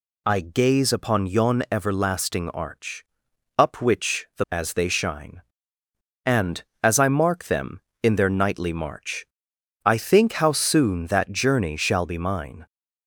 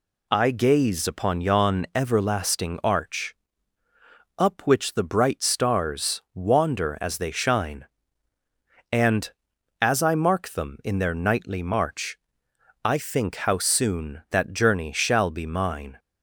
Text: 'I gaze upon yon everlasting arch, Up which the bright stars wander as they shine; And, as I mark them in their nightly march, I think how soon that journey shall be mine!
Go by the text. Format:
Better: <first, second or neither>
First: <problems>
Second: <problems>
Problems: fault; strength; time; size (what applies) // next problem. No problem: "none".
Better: second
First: skips "bright stars wander"; at 4.4 s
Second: none